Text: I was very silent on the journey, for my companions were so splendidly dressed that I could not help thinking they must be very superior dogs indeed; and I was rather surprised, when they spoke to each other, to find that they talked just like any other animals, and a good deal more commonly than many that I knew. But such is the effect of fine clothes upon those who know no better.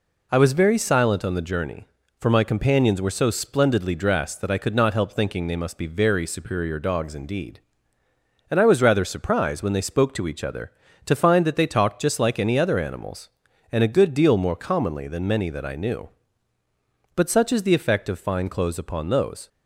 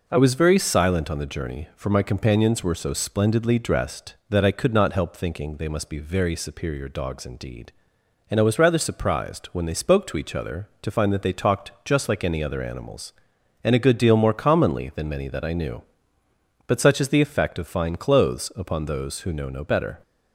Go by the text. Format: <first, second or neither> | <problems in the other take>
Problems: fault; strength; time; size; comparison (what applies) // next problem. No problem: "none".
second | stops before "who know no better"; at 19.4 s